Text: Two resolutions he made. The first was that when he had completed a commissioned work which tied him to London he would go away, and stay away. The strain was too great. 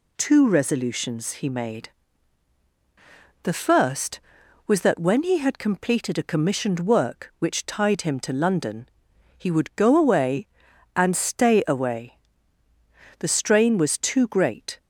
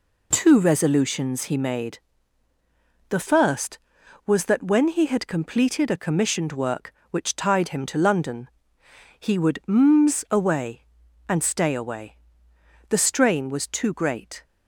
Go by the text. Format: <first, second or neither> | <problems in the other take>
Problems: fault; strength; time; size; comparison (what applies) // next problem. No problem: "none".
first | pauses between "London" and "he"; noticeable; at 8.4 s; 0.72 s long; noticeable in the first // says "mms" for "go"; at 9.6 s